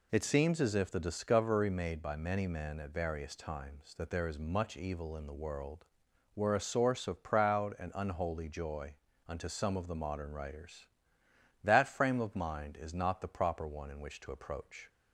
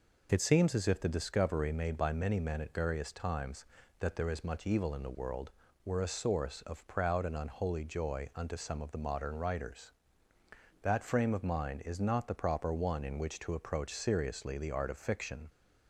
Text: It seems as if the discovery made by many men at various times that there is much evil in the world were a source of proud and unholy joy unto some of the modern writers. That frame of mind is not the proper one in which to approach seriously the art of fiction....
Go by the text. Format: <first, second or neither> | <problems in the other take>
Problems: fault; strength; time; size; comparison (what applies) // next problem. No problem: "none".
second | pauses between "joy" and "unto"; slight; at 8.9 s; 0.30 s long // stops before "seriously the art of fiction"; at 14.8 s